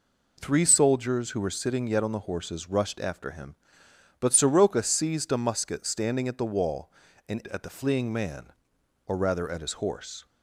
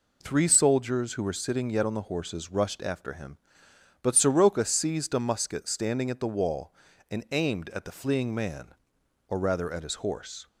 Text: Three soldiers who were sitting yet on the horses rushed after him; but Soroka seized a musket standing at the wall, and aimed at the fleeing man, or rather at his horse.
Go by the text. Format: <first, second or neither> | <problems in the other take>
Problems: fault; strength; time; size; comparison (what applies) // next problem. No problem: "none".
second | skips "aimed"; at 7.4 s